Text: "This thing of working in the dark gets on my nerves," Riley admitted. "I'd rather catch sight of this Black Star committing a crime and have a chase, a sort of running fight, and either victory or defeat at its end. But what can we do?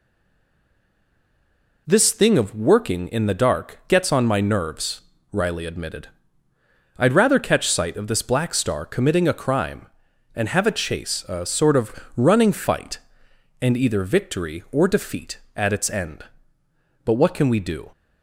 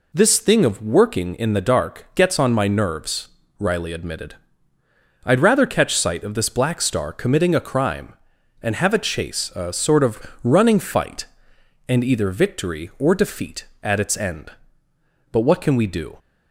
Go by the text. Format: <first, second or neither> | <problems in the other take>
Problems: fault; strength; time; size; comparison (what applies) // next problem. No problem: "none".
second | stays silent before the first word; noticeable; until 1.8 s; 1.8 s long // pauses between "of" and "running"; slight; at 11.9 s; 0.22 s long; slight in the second